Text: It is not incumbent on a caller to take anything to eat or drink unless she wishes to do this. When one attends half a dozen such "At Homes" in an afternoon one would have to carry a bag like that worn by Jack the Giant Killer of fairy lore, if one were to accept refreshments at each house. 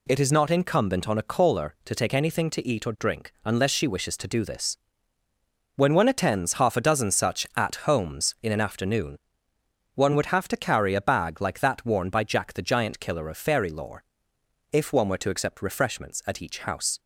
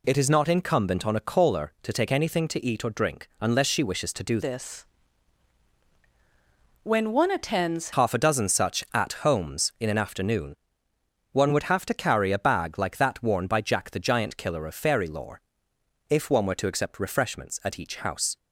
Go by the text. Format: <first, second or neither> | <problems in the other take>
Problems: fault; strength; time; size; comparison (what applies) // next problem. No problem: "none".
first | changes voice from "this" to "attends"; from 4.4 to 7.9 s; 3.5 s long // pauses between "afternoon" and "one"; noticeable; at 10.5 s; 0.76 s long; noticeable in the first